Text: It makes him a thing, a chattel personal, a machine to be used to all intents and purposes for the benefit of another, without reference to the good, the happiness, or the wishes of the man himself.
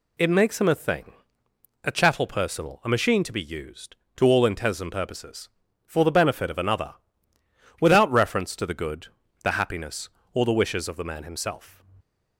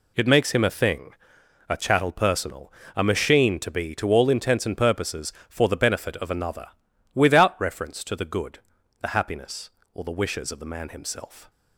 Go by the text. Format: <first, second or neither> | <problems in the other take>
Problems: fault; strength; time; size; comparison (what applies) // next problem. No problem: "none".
first | skips "used"; at 3.9 s